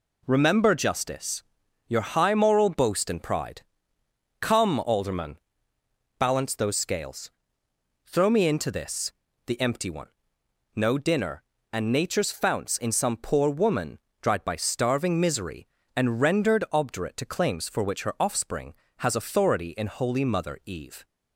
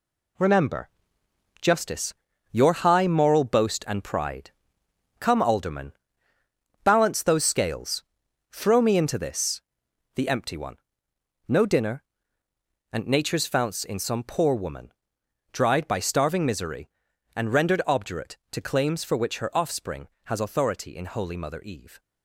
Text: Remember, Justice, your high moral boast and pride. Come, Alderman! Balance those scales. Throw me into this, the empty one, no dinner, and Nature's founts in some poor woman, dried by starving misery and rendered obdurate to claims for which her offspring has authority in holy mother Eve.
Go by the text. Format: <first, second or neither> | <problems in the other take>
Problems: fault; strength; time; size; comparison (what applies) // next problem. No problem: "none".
first | gets quieter; strong; throughout; 7.5 dB